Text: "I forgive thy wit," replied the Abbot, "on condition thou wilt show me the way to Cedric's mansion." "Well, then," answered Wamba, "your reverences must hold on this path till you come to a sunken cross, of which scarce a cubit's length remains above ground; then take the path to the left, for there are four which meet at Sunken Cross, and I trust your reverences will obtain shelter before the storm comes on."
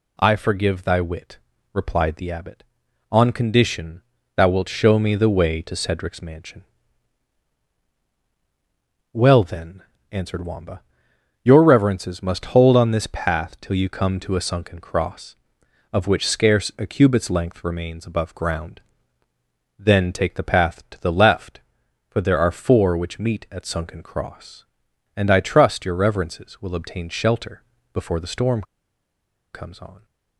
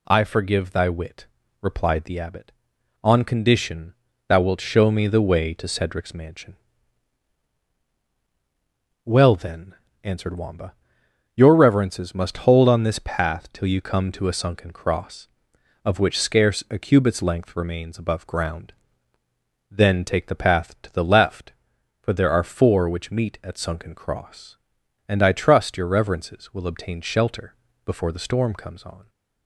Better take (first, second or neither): second